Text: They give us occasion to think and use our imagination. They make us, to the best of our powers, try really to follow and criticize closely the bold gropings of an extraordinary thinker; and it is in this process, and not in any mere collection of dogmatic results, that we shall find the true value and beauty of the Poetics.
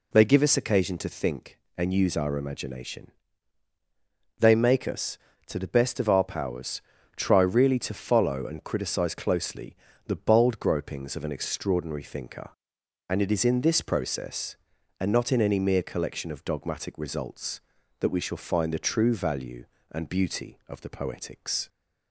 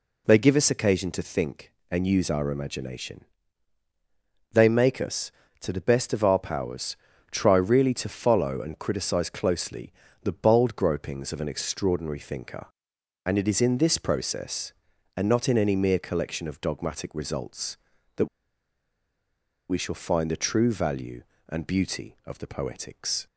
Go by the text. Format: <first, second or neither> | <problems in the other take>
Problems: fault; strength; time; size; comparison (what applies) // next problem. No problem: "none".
first | pauses between "closely" and "the"; slight; at 9.9 s; 0.30 s long; slight in the first // pauses between "that" and "we"; strong; at 18.2 s; 1.4 s long